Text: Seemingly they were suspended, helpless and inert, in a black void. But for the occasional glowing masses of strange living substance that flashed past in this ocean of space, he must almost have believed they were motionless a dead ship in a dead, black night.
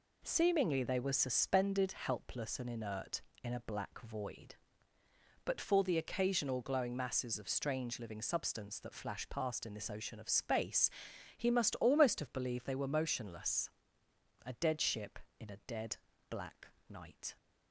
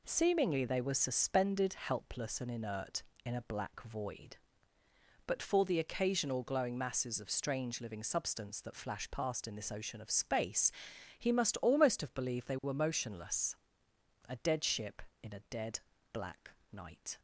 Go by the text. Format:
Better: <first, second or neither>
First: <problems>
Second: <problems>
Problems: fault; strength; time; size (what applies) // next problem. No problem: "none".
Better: neither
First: pauses between "motionless" and "a"; noticeable; at 13.6 s; 0.79 s long // pauses between "black" and "night"; slight; at 16.6 s; 0.20 s long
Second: pauses between "motionless" and "a"; noticeable; at 13.5 s; 0.76 s long // pauses between "black" and "night"; slight; at 16.5 s; 0.20 s long